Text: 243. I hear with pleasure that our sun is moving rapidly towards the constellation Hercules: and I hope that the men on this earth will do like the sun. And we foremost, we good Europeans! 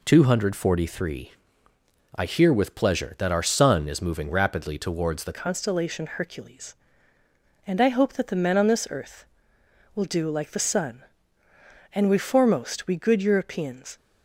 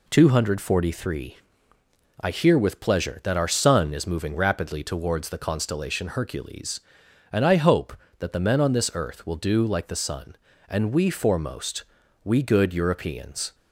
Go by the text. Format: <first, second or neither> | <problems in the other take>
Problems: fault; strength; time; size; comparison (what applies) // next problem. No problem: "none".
second | changes voice at "constellation"; from 5.3 s on; 8.6 s long